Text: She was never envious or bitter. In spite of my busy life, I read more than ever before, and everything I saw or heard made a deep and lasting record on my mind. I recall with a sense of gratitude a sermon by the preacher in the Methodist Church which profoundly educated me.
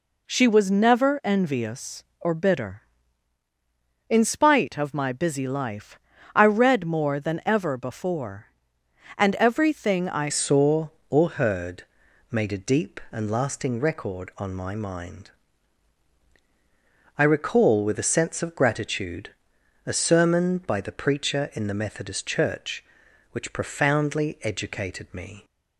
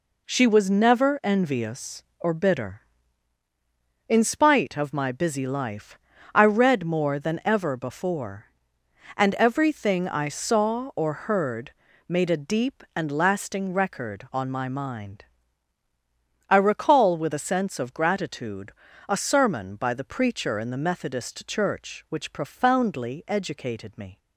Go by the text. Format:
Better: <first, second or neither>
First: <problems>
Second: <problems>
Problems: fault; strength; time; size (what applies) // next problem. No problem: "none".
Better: second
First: changes voice at "saw"; from 10.2 s on; 15.2 s long // pauses between "heard" and "made"; noticeable; at 11.8 s; 0.46 s long // pauses between "gratitude" and "a"; noticeable; at 19.3 s; 0.56 s long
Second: pauses between "heard" and "made"; slight; at 11.7 s; 0.36 s long // pauses between "gratitude" and "a"; slight; at 18.7 s; 0.36 s long